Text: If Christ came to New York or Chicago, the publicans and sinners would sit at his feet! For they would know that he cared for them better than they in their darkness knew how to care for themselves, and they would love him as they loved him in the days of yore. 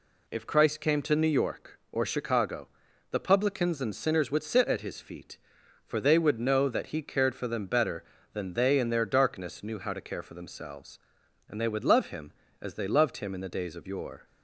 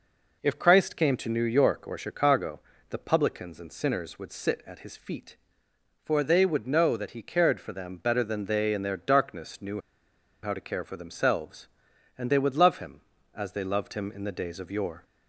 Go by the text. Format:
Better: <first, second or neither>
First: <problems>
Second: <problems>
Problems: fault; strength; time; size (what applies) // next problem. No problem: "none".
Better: first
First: none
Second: pauses between "knew" and "how"; noticeable; at 9.8 s; 0.62 s long